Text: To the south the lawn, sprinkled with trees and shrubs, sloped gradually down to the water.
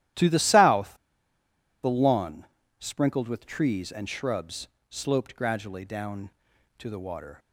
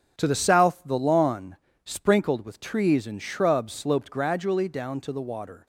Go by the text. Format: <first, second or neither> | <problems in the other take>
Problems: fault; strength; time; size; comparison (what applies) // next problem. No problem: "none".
second | starts louder than the rest; strong; until 2.0 s; 13 dB; strong in the second // pauses between "south" and "the"; noticeable; at 0.9 s; 0.90 s long